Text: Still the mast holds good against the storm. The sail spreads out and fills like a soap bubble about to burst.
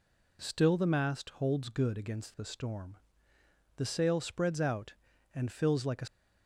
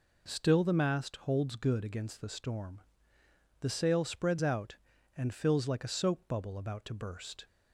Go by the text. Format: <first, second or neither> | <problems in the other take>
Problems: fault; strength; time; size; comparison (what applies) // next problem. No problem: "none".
second | stops before "soap bubble about to burst"; at 6.0 s